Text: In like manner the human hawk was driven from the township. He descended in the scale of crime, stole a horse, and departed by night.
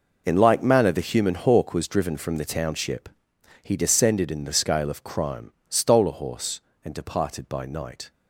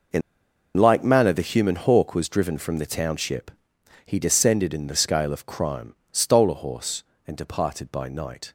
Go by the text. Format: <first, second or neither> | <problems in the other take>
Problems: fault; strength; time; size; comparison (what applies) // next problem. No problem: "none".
first | pauses between "In" and "like"; noticeable; at 0.2 s; 0.55 s long